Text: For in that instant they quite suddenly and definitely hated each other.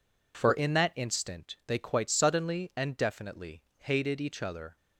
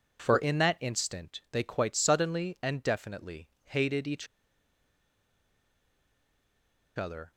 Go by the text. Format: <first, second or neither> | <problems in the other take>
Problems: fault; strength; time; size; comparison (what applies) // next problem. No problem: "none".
first | pauses between "definitely" and "hated"; slight; at 3.4 s; 0.16 s long; slight in the first // pauses between "each" and "other"; strong; at 4.2 s; 2.7 s long